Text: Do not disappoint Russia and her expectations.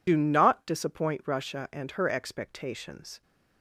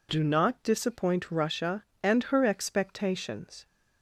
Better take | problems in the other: second | loses the start of "Do"; at 0.0 s; 55 ms

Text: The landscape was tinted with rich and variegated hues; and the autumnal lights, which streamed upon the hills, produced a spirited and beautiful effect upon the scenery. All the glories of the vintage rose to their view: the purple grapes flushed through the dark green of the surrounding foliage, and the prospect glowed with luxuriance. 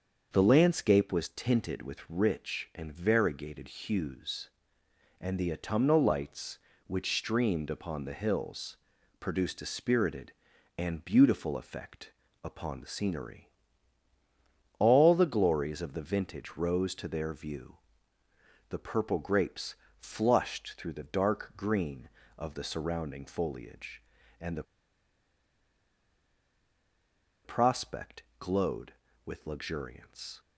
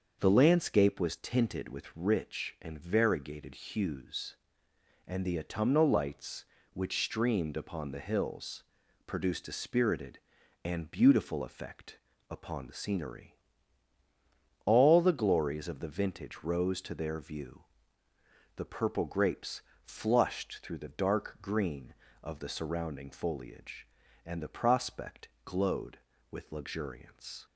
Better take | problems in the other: second | starts louder than the rest; until 1.3 s; 6.5 dB; also in the second // pauses between "effect" and "upon"; slight; at 12.1 s; 0.30 s long; slight in the second // pauses between "grapes" and "flushed"; slight; at 19.7 s; 0.24 s long; slight in the second // pauses between "the" and "prospect"; strong; at 24.6 s; 2.8 s long // pauses between "prospect" and "glowed"; slight; at 28.2 s; 0.18 s long; slight in the second

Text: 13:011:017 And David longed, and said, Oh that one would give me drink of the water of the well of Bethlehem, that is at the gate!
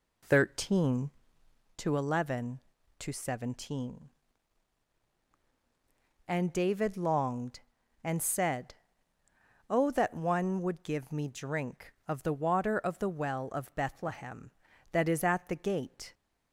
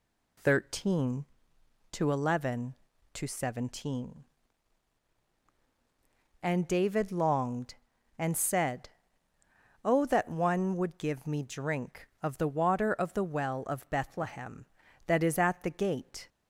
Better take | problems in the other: second | starts louder than the rest; slight; until 1.7 s; 2.5 dB

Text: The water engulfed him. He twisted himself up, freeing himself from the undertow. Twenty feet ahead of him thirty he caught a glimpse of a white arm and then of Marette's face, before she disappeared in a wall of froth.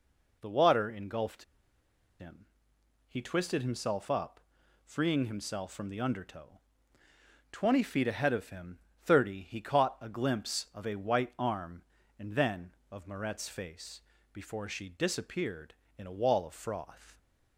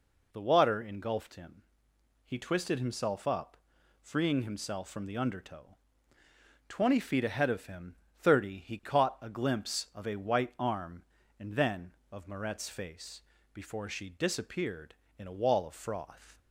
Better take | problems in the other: second | pauses between "engulfed" and "him"; noticeable; at 1.4 s; 0.76 s long // pauses between "him" and "thirty"; slight; at 8.7 s; 0.26 s long; slight in the second

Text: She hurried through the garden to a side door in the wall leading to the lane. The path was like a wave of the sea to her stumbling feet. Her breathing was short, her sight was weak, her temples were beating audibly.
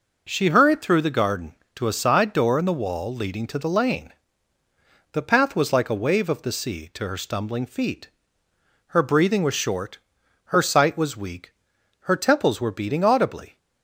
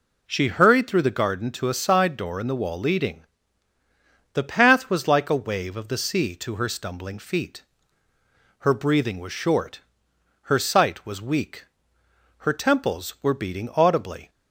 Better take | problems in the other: first | skips "to the lane"; at 3.7 s

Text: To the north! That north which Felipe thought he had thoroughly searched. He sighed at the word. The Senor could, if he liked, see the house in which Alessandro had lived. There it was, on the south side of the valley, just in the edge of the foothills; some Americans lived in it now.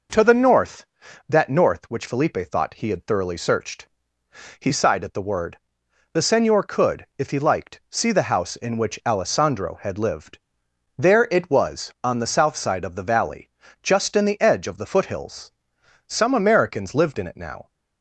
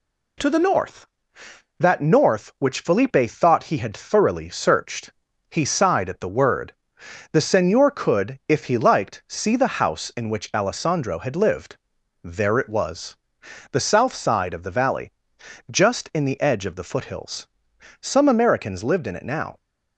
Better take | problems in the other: first | skips "on"; at 13.4 s

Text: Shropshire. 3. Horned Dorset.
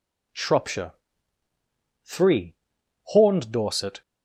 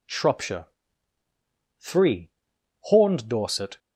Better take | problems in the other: neither | none

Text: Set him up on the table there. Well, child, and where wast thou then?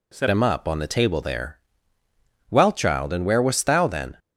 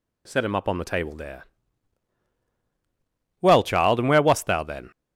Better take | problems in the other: second | changes voice at "him"; from 0.3 s on; 3.8 s long

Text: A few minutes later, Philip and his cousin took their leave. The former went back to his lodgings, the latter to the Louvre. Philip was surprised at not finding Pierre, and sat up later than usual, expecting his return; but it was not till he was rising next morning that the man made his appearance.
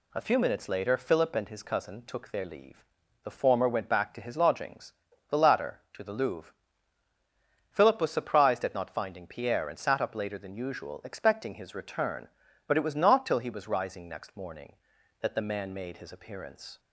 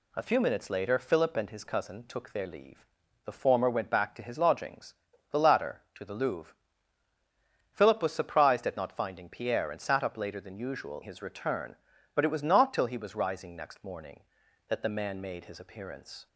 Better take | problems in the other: first | skips "expecting"; at 11.0 s

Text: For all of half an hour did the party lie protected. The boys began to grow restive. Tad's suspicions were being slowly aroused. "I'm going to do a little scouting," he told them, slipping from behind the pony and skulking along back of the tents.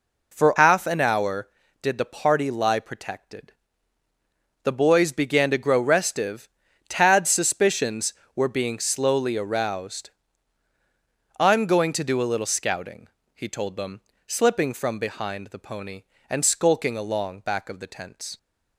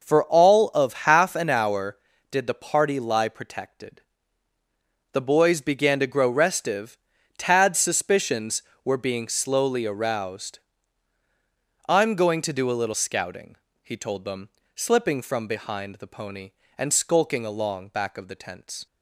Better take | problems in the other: second | skips "all of"; at 0.5 s

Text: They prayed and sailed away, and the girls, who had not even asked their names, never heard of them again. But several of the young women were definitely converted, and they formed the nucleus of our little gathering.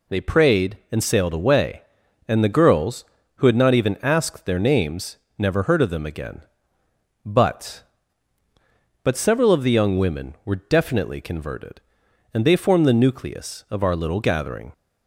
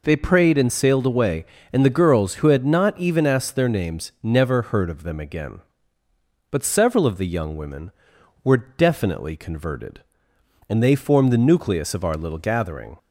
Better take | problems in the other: second | says "But" twice; at 9.0 s

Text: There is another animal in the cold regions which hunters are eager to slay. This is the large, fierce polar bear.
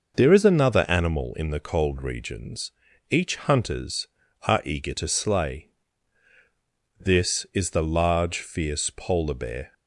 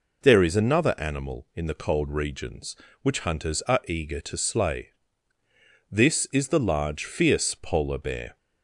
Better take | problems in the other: second | starts louder than the rest; noticeable; until 1.1 s; 6 dB // says "each" for "which"; at 3.0 s

